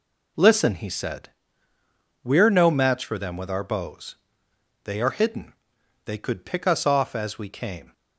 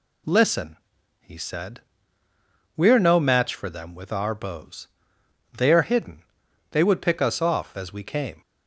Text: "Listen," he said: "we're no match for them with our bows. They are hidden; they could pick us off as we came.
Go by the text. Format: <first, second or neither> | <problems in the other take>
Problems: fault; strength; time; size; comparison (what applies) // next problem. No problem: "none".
first | says "would" for "could"; at 6.8 s